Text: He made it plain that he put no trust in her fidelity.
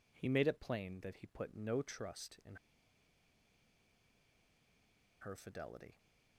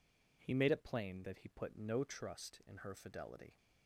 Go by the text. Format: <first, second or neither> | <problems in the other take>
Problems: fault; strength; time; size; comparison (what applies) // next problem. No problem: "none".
second | pauses between "in" and "her"; strong; at 2.5 s; 2.6 s long